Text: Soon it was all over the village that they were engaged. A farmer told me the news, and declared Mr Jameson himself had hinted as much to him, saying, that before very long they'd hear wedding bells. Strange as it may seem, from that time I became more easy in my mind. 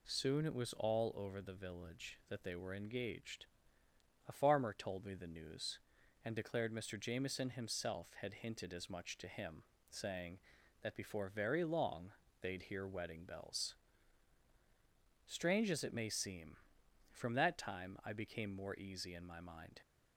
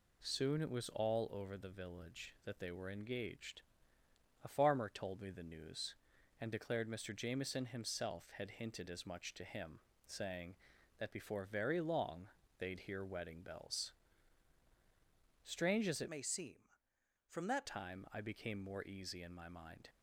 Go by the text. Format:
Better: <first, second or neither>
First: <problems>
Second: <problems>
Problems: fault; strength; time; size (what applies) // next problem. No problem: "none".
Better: first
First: pauses between "long" and "they'd"; slight; at 12.1 s; 0.31 s long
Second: pauses between "long" and "they'd"; slight; at 12.2 s; 0.32 s long // changes voice from "may" to "that"; from 16.0 to 17.6 s; 1.6 s long